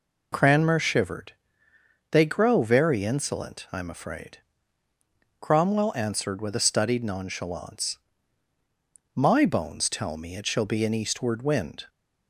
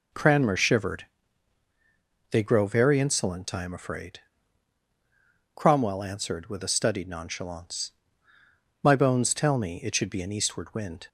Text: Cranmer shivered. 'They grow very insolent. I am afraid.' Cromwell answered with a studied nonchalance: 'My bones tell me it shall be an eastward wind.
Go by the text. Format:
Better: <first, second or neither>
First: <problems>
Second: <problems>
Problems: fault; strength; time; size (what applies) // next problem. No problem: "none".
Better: first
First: none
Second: says "should" for "shall"; at 9.9 s